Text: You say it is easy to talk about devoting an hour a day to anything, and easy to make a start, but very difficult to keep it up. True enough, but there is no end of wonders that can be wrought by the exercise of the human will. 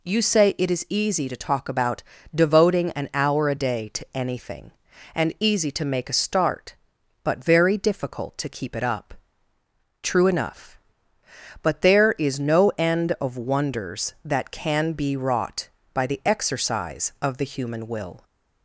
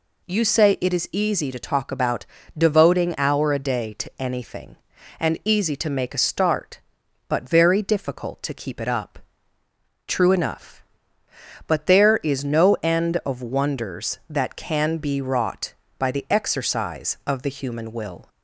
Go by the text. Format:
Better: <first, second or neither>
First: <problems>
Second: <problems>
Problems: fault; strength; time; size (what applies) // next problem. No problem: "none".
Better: first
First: pauses between "about" and "devoting"; slight; at 2.0 s; 0.32 s long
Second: pauses between "about" and "devoting"; slight; at 2.2 s; 0.32 s long // skips "an"; at 3.1 s